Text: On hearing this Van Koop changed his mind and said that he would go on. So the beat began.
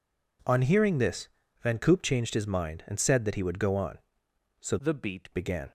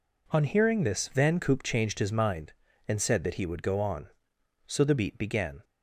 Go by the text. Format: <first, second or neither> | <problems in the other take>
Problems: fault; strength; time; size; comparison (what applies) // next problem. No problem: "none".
second | pauses between "this" and "Van"; slight; at 1.2 s; 0.32 s long // changes voice from "the" to "beat"; from 4.7 to 5.3 s; 0.6 s long